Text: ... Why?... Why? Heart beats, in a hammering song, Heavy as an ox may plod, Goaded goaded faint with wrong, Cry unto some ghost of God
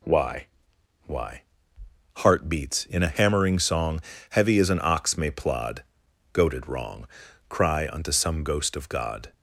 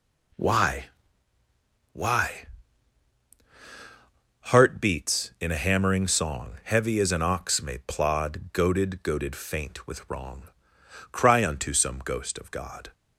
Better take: second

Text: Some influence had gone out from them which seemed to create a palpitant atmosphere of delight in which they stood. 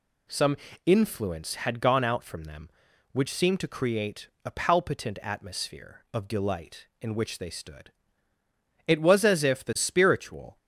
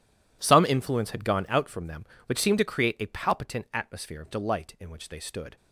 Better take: second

